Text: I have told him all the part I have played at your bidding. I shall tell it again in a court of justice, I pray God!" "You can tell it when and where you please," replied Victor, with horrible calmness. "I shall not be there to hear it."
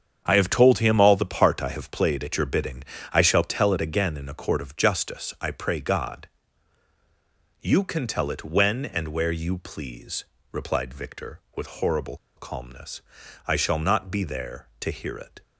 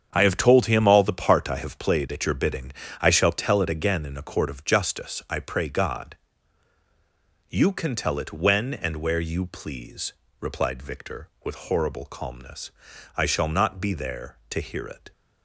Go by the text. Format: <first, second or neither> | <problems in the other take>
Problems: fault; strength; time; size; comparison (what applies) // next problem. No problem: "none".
second | starts louder than the rest; strong; until 1.2 s; 7.5 dB; strong in the second // pauses between "horrible" and "calmness"; slight; at 12.1 s; 0.21 s long